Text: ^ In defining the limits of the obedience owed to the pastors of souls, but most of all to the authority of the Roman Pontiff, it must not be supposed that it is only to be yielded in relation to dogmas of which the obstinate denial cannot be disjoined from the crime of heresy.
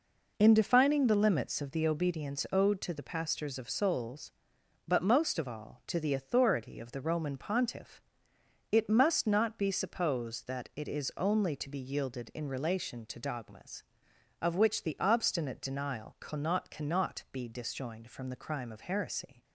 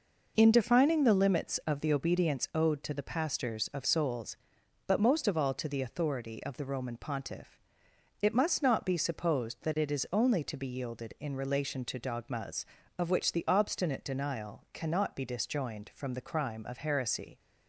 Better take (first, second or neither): second